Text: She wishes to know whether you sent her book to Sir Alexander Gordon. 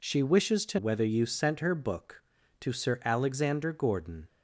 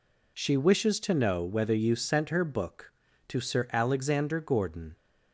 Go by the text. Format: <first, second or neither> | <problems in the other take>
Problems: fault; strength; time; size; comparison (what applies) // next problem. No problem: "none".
second | skips "know"; at 0.7 s